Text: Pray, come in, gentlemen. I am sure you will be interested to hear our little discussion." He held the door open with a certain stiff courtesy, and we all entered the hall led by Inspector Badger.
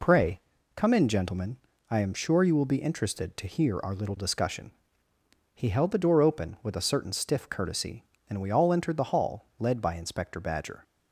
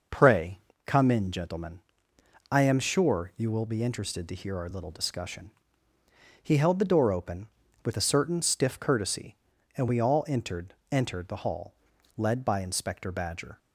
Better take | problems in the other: first | says "entered" twice; at 10.9 s // pauses between "hall" and "led"; at 11.7 s; 0.44 s long

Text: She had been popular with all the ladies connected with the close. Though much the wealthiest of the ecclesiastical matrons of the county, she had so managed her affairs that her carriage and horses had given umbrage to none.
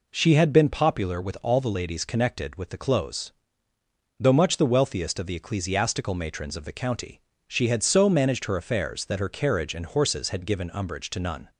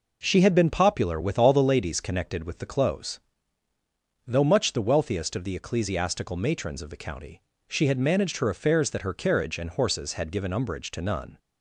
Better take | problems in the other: first | skips "so"; at 7.9 s

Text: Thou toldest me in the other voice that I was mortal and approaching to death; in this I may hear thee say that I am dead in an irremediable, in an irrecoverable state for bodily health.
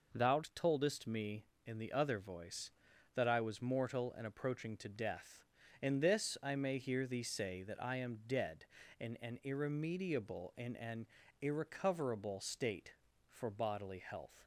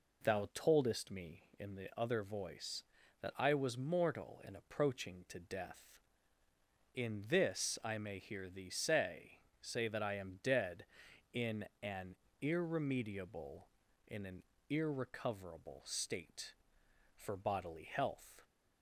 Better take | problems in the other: first | says "say" twice; at 9.5 s // pauses between "in" and "an"; slight; at 11.6 s; 0.18 s long // pauses between "an" and "irremediable"; slight; at 12.1 s; 0.26 s long // pauses between "an" and "irrecoverable"; slight; at 14.4 s; 0.28 s long; slight in the first

